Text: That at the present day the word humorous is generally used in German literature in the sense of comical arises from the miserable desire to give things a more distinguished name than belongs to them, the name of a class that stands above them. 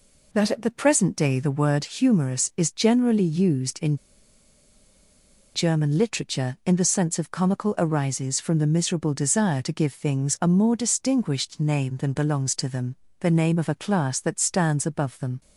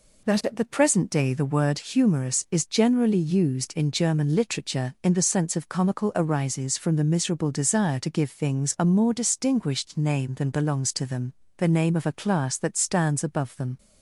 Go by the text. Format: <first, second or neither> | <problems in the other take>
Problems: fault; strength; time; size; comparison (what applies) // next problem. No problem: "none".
second | pauses between "in" and "German"; strong; at 3.9 s; 1.5 s long